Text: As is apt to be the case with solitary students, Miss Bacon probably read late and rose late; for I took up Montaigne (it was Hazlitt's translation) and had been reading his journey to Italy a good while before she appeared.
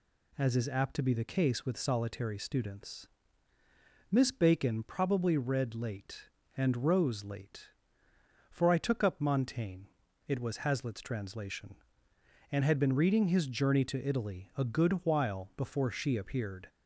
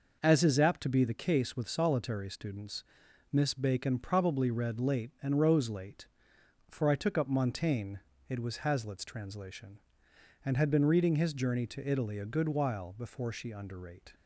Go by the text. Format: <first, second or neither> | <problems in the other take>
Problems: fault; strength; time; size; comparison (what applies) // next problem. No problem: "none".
first | says "underrate" for "appeared"; at 13.5 s